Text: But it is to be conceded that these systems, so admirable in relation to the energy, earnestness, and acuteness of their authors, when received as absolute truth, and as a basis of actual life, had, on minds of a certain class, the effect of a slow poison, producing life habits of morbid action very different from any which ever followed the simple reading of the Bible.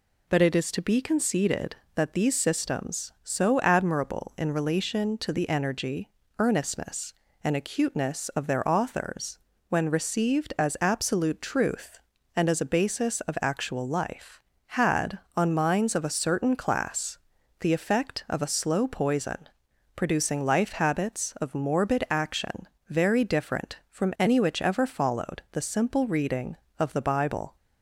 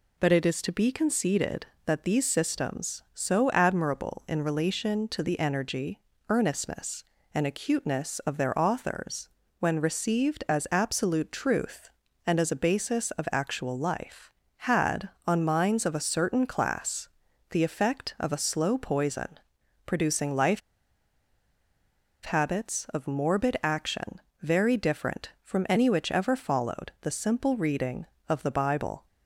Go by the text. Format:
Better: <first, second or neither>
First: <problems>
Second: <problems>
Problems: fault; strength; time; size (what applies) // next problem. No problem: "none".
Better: first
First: pauses between "action" and "very"; slight; at 22.6 s; 0.22 s long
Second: pauses between "life" and "habits"; strong; at 20.6 s; 1.6 s long // pauses between "action" and "very"; slight; at 24.1 s; 0.22 s long